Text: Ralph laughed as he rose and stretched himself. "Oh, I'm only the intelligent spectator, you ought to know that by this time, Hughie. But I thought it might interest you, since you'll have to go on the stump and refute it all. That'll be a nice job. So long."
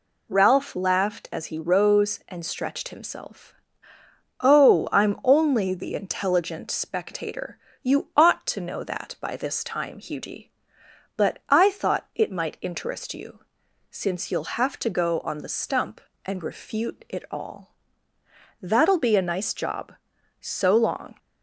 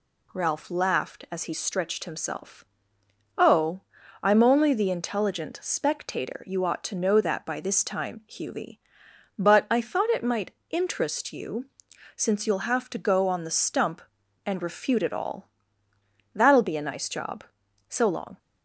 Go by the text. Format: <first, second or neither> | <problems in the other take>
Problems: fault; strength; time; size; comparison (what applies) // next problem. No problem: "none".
first | skips "rose and"; at 1.5 s // pauses between "might" and "interest"; slight; at 10.5 s; 0.16 s long